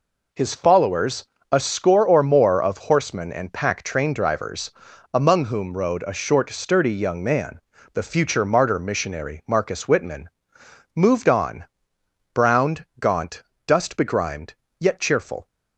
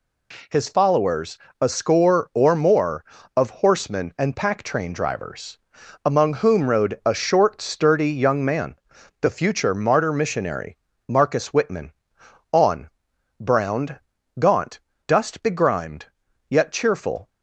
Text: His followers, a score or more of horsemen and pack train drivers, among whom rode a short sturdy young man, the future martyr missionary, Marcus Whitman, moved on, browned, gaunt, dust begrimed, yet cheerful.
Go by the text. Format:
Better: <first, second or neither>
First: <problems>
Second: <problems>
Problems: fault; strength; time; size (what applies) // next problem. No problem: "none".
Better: first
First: none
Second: skips "moved"; at 12.2 s